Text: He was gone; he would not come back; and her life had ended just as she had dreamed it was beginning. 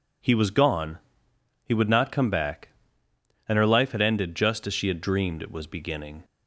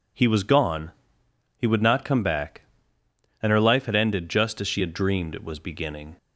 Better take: neither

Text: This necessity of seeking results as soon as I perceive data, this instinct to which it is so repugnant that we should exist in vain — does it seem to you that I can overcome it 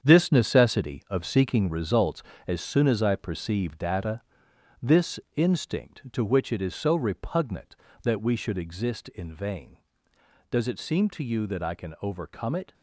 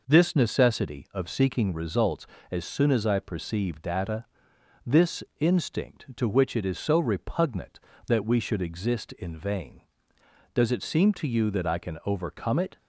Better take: second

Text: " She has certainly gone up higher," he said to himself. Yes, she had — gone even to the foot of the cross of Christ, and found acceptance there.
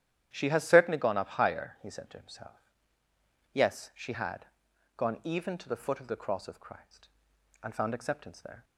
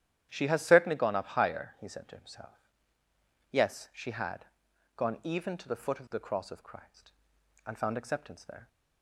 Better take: neither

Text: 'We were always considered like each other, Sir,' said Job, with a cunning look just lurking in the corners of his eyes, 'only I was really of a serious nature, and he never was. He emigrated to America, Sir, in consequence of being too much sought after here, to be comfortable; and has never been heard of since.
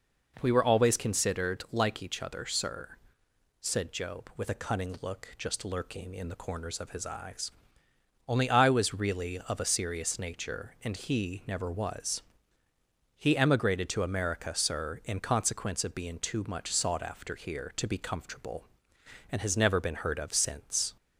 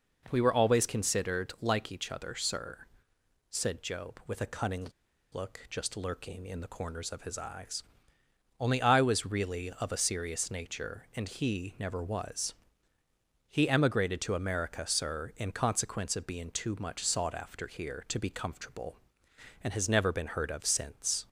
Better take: first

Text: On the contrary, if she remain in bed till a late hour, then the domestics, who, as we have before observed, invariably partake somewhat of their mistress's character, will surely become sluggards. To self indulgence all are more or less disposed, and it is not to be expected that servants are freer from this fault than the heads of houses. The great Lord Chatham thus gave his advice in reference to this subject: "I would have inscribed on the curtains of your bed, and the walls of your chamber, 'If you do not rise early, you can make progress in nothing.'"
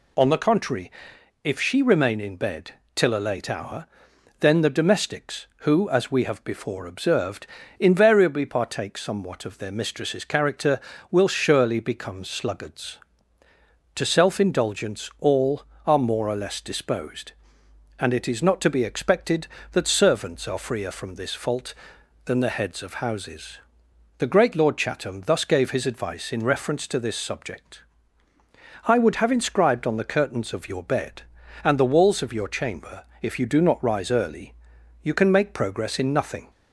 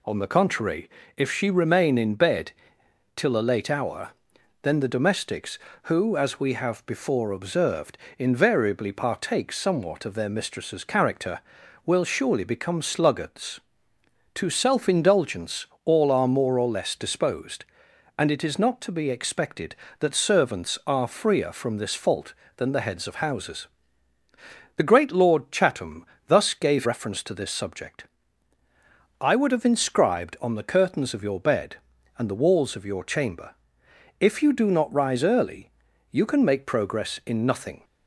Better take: first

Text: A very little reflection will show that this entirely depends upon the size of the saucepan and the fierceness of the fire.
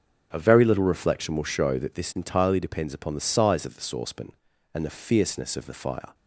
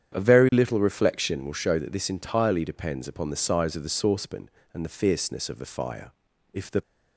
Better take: first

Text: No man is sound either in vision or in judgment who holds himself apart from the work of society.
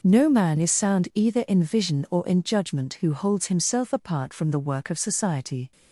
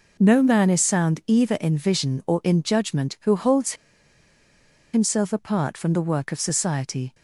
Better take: first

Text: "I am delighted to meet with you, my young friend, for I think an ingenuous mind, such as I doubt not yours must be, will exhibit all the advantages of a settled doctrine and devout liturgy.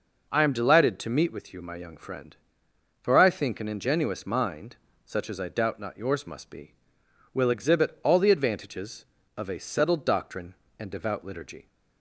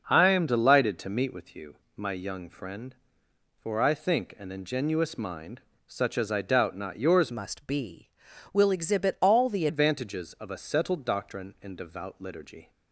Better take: first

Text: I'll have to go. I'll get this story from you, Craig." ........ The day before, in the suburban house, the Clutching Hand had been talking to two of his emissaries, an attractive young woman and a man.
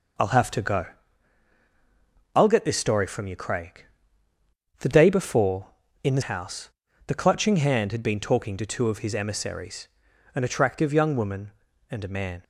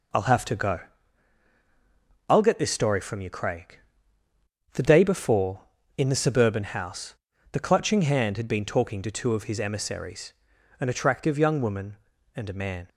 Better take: second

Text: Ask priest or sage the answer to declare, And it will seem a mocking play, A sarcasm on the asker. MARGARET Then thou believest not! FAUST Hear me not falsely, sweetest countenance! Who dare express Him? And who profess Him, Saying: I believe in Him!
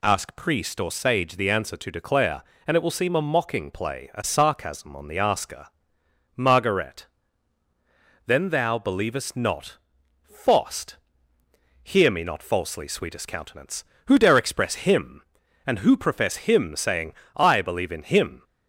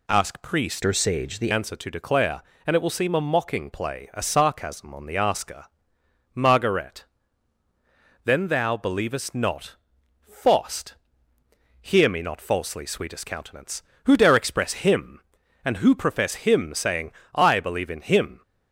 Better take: first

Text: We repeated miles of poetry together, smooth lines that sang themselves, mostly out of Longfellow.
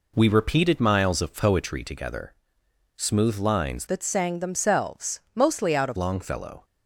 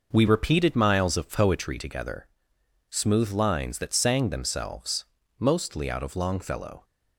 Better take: second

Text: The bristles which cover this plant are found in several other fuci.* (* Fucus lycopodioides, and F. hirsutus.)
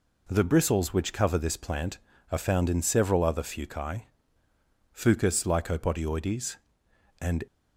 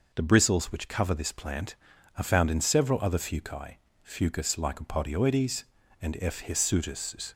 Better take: second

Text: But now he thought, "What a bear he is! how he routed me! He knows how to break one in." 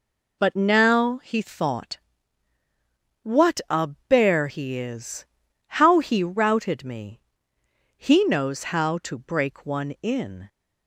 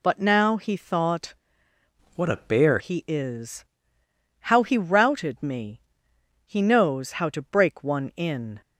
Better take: first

